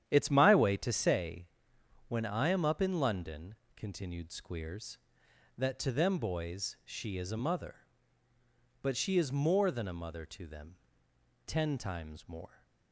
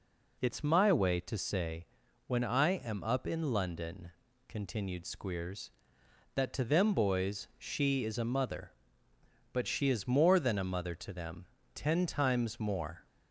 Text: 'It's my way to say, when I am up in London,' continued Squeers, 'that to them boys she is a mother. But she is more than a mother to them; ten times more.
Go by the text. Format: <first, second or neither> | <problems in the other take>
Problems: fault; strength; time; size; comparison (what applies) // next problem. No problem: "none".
second | starts louder than the rest; strong; until 1.1 s; 10 dB